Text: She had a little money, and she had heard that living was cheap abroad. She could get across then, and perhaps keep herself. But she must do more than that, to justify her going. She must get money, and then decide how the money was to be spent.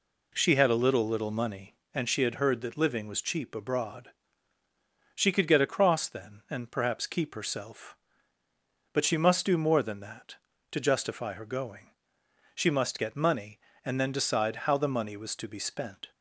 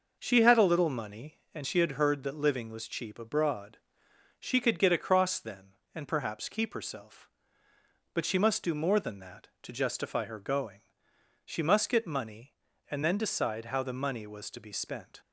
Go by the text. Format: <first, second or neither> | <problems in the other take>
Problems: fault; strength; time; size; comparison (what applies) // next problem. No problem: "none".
second | says "little" twice; at 1.0 s